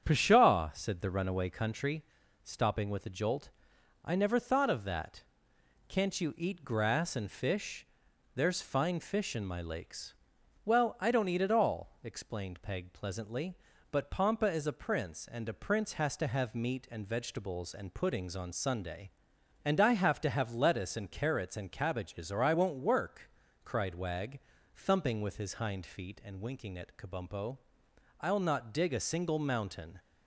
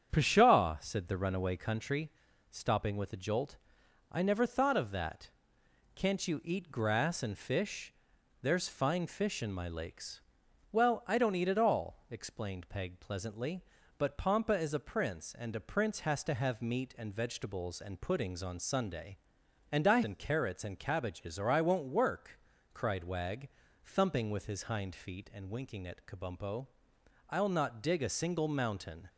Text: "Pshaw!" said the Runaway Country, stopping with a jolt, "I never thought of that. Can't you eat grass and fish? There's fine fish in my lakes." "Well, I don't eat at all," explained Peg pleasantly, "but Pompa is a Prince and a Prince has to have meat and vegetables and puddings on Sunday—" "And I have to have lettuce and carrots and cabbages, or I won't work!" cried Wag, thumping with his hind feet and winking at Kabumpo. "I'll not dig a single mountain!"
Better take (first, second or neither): first